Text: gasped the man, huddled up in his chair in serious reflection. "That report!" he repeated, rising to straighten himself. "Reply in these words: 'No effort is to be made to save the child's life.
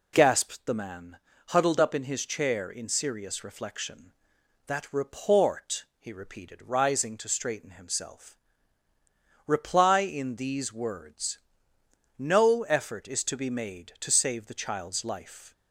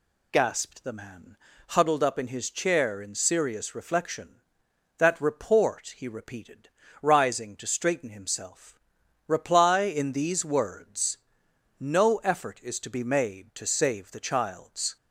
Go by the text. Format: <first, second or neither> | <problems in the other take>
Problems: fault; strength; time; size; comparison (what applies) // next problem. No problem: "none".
first | stops before "life"; at 14.9 s